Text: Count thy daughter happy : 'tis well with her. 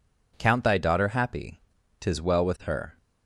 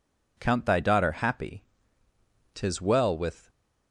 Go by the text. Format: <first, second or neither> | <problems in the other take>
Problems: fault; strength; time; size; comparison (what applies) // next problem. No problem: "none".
first | stops before "her"; at 3.4 s